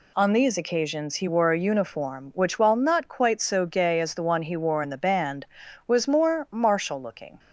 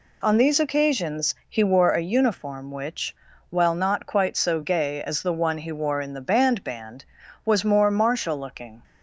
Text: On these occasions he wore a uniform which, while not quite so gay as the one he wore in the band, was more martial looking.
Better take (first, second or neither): first